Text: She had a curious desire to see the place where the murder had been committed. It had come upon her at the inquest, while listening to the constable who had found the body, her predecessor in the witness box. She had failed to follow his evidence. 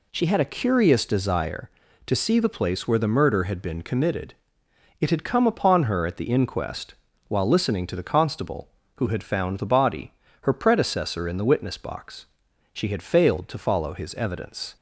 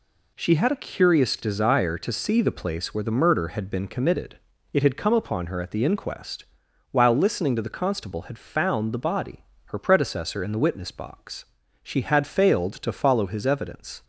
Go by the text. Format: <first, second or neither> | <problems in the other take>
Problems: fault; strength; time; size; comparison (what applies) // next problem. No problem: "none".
first | skips "who"; at 8.2 s